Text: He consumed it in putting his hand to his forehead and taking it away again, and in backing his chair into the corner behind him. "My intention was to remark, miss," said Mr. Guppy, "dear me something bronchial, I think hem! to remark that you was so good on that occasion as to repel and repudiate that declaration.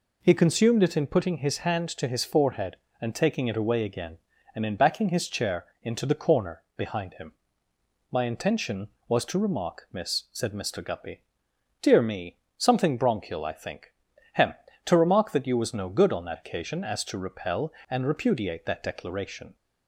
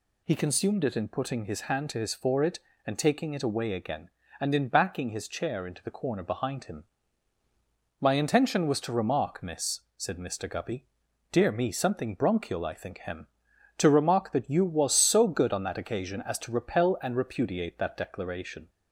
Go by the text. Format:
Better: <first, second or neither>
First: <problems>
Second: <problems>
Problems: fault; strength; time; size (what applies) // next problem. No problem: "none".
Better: second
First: pauses between "chair" and "into"; slight; at 5.6 s; 0.16 s long // pauses between "corner" and "behind"; slight; at 6.6 s; 0.16 s long // pauses between "me" and "something"; slight; at 12.3 s; 0.18 s long // pauses between "think" and "hem"; at 13.9 s; 0.40 s long // says "no" for "so"; at 15.7 s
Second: none